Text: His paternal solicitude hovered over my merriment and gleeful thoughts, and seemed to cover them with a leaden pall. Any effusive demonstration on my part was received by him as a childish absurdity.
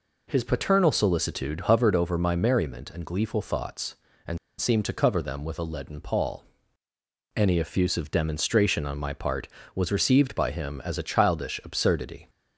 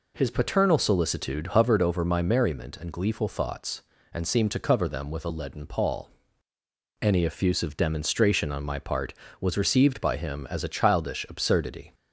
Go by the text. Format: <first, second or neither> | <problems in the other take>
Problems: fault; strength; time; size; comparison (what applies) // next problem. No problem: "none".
second | pauses between "and" and "seemed"; slight; at 4.3 s; 0.21 s long